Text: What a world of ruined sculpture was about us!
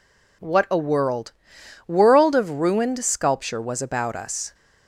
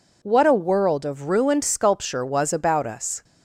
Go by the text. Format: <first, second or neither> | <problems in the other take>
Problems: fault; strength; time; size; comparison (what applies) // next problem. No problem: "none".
second | says "world" twice; at 1.8 s